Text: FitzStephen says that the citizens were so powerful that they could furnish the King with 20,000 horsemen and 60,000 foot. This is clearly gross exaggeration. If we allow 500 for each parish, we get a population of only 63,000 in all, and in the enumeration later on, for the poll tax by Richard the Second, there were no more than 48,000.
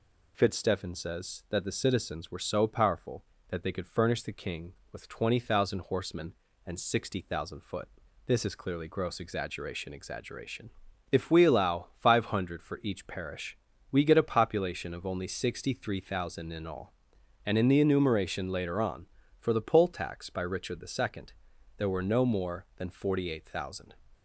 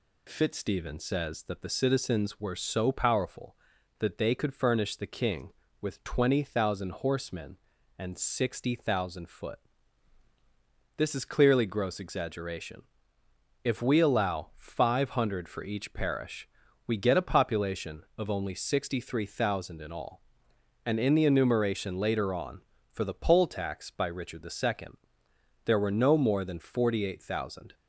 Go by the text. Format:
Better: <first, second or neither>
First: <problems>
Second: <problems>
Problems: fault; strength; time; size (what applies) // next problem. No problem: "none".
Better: second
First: says "exaggeration" twice; at 9.9 s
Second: none